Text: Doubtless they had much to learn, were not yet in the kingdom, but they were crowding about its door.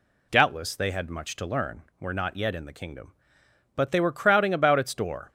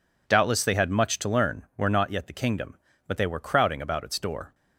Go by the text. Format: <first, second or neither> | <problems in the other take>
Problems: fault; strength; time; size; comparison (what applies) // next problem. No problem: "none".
first | skips "in"; at 2.2 s